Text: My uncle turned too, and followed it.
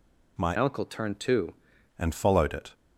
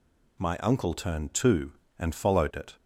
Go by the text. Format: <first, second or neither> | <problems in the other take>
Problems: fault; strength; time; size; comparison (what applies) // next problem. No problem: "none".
second | changes voice from "uncle" to "too"; from 0.5 to 1.5 s; 1.0 s long